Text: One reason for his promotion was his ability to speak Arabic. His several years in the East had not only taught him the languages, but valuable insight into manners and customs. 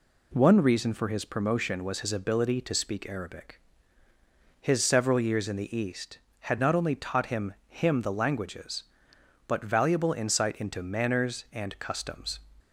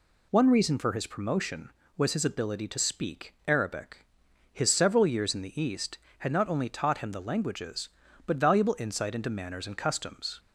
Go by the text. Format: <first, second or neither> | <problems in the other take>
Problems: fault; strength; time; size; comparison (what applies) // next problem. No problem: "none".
second | says "him" twice; at 7.6 s